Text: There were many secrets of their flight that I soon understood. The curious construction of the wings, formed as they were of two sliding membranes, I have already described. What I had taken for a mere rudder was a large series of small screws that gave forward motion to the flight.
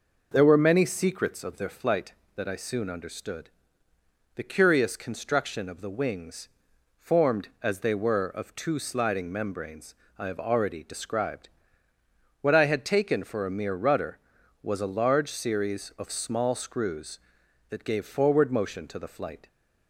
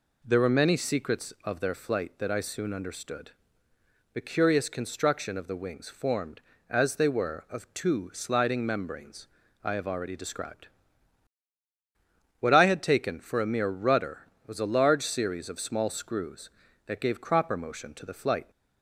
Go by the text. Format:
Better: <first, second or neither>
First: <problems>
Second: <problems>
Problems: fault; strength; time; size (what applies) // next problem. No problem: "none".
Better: first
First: none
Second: says "cropper" for "forward"; at 17.1 s